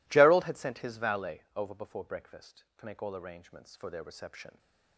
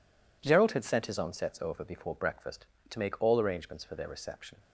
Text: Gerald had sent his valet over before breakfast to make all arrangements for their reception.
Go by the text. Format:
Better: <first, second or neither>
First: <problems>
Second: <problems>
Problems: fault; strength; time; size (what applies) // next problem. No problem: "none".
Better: first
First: none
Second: says "onsets" for "valet"; at 1.1 s